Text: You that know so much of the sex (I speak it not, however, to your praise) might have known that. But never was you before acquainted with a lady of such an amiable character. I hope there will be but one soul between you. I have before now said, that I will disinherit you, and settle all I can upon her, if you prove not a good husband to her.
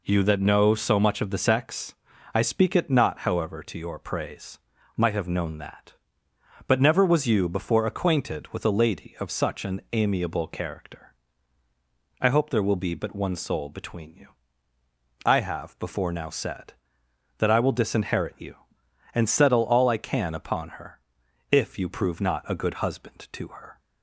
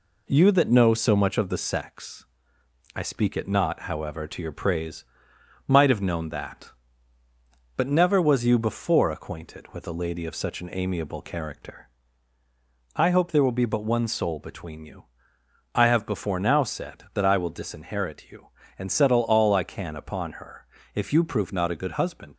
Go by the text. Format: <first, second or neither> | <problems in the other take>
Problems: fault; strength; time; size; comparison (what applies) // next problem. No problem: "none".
first | stops before "to her"; at 22.3 s